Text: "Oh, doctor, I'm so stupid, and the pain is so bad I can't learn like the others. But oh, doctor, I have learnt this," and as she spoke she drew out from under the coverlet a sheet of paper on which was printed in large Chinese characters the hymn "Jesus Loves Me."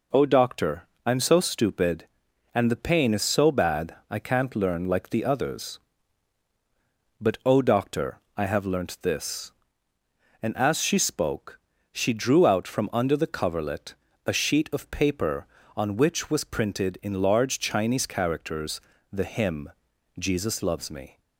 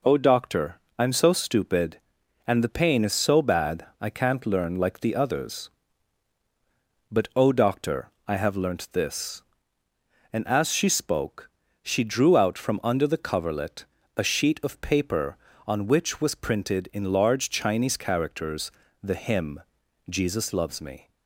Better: neither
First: pauses between "spoke" and "she"; slight; at 11.5 s; 0.32 s long // pauses between "coverlet" and "a"; slight; at 13.9 s; 0.32 s long // pauses between "characters" and "the"; slight; at 18.7 s; 0.32 s long // pauses between "hymn" and "Jesus"; noticeable; at 19.6 s; 0.48 s long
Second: pauses between "spoke" and "she"; slight; at 11.5 s; 0.32 s long // pauses between "coverlet" and "a"; slight; at 13.8 s; 0.32 s long // pauses between "characters" and "the"; slight; at 18.7 s; 0.32 s long // pauses between "hymn" and "Jesus"; noticeable; at 19.6 s; 0.48 s long

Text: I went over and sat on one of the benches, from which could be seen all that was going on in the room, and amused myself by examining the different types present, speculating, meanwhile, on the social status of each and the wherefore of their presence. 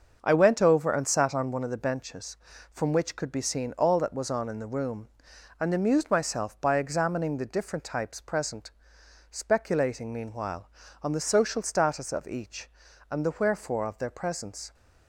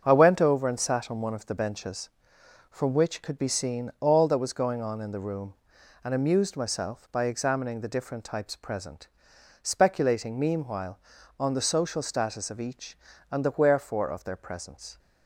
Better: second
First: starts louder than the rest; until 1.2 s; 6.5 dB // skips "going"; at 4.2 s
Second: starts louder than the rest; until 1.0 s; 7 dB

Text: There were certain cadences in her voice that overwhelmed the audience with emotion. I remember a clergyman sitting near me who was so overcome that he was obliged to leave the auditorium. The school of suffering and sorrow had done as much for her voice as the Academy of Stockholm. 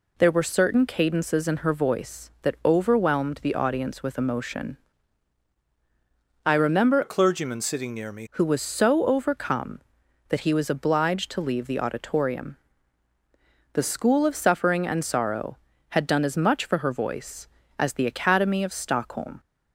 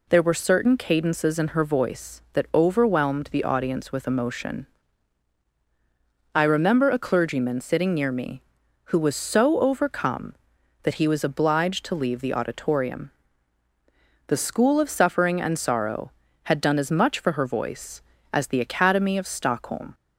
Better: second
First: changes voice from "a" to "me"; from 7.0 to 8.2 s; 1.2 s long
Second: none

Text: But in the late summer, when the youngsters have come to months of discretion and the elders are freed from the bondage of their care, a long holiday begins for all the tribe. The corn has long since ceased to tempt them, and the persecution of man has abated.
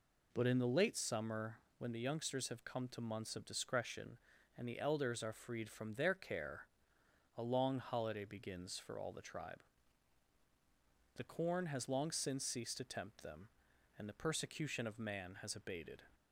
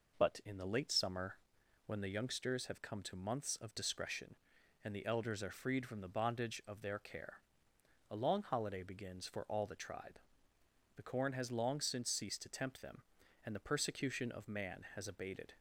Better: second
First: skips "the bondage of"; at 5.9 s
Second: none

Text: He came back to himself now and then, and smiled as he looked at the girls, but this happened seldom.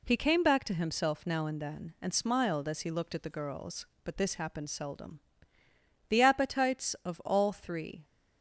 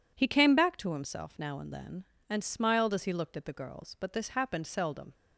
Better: second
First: goes on to say "The appetites of all three"; strong; from 6.1 s on; 1.9 s long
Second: none

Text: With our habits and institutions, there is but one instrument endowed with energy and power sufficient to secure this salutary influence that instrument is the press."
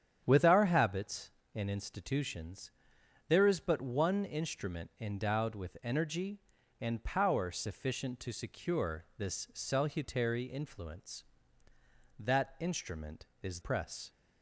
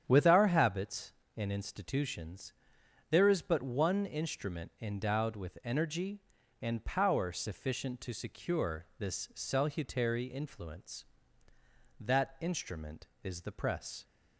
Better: second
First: starts louder than the rest; strong; until 1.2 s; 9 dB // skips "the"; at 13.6 s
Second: starts louder than the rest; strong; until 1.0 s; 9 dB

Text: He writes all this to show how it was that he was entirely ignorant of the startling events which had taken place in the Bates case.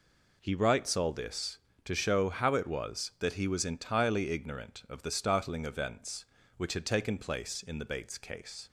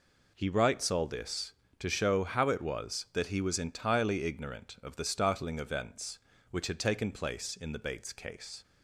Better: neither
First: none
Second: none

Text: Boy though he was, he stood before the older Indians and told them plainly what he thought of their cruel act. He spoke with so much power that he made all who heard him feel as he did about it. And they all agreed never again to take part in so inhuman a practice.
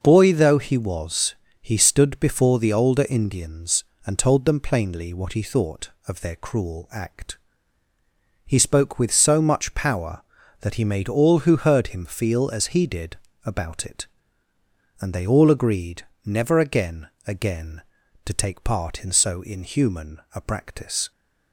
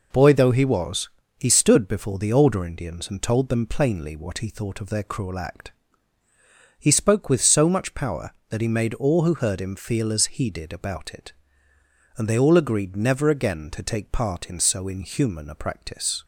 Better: second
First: pauses between "did" and "about"; slight; at 13.1 s; 0.28 s long // pauses between "agreed" and "never"; slight; at 16.0 s; 0.24 s long // says "again" twice; at 17.2 s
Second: none

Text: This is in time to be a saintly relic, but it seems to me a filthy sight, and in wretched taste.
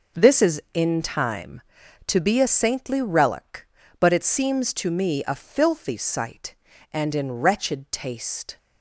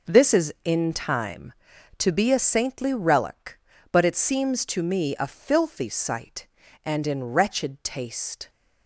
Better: neither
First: none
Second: none

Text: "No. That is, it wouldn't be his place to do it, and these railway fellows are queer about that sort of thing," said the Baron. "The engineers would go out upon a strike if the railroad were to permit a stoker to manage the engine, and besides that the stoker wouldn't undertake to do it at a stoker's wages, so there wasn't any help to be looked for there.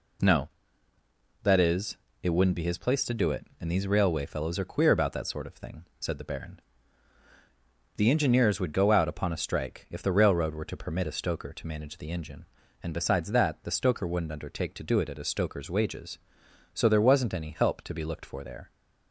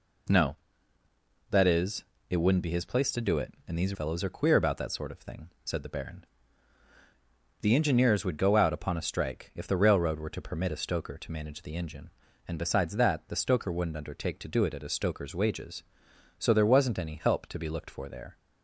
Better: first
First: none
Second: skips "railway"; at 3.9 s

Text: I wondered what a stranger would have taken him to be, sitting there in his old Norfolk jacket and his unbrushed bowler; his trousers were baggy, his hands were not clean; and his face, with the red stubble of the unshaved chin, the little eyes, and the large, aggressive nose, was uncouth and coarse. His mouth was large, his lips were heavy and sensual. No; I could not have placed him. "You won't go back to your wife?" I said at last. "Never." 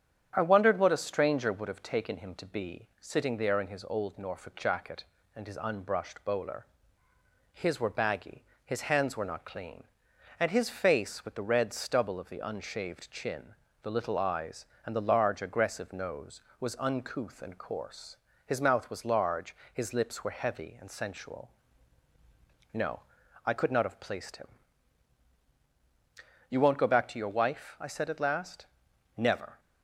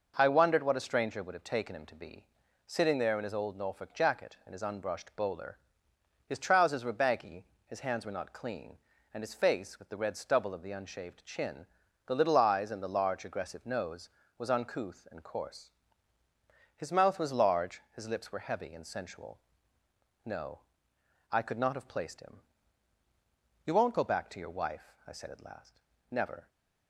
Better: second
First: starts louder than the rest; strong; until 1.3 s; 8.5 dB // skips "trousers"; at 7.7 s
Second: none

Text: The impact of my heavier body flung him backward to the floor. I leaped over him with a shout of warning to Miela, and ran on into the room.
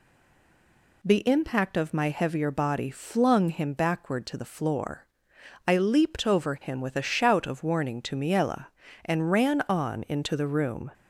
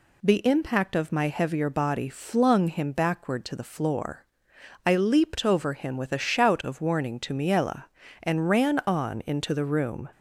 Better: second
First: stays silent before the first word; until 1.0 s; 1.0 s long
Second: none

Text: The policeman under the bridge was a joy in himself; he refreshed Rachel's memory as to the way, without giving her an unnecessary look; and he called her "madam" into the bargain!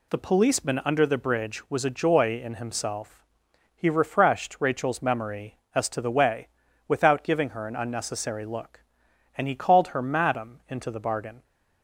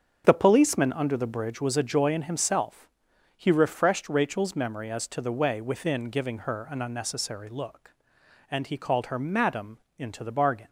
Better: first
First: none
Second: starts louder than the rest; strong; until 1.2 s; 7.5 dB // says "within" for "without"; at 5.6 s // pauses between "madam" and "into"; slight; at 9.7 s; 0.22 s long

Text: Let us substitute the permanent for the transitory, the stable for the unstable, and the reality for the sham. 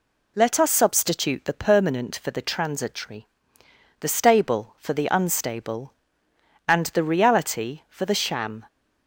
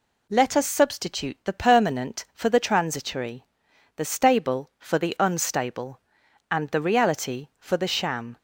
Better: neither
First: none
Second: none

